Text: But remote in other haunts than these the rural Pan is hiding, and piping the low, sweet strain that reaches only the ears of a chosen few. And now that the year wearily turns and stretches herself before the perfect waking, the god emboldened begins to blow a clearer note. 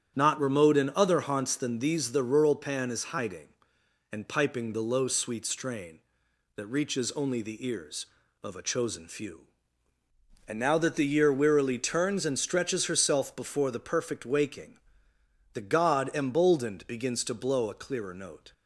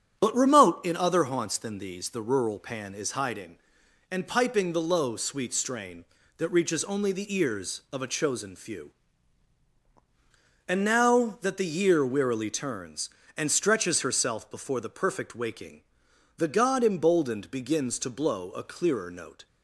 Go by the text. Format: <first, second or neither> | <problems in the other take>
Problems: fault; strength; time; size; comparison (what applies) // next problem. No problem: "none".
second | starts louder than the rest; strong; until 1.1 s; 8 dB; strong in the second // says "Not" for "But"; at 0.1 s